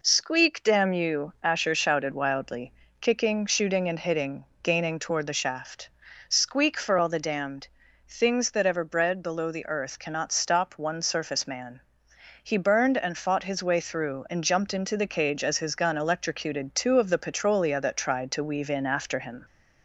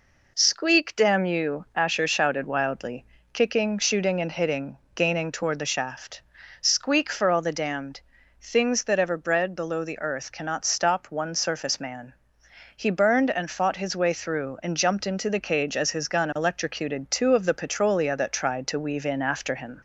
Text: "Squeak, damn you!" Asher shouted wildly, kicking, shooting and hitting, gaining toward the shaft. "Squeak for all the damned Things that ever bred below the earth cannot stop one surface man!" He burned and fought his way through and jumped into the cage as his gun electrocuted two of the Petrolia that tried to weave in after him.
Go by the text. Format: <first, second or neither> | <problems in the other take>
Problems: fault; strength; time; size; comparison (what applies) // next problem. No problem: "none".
neither | pauses between "damned" and "Things"; the same in both